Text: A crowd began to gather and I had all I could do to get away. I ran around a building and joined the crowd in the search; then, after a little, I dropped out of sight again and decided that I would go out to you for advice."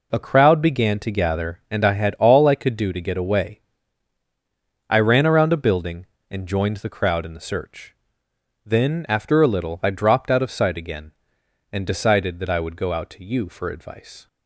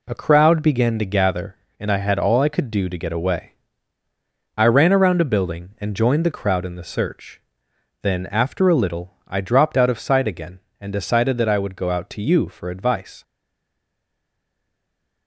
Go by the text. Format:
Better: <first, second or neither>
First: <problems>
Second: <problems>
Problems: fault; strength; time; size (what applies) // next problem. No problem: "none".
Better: first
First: none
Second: stays silent after the last word; noticeable; from 13.2 s on; 2.0 s long